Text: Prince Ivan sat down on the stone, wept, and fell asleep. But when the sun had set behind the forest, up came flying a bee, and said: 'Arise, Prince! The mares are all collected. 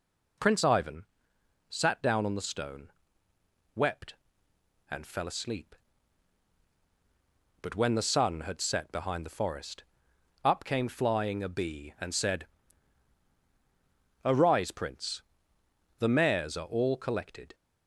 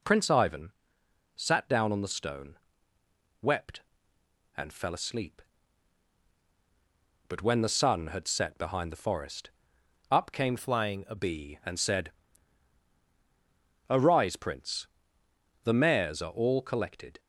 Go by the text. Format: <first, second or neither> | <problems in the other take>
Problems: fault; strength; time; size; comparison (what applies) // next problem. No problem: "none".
first | pauses between "Ivan" and "sat"; noticeable; at 0.7 s; 0.64 s long; noticeable in the first // changes voice from "flying" to "a"; from 10.5 to 11.1 s; 0.6 s long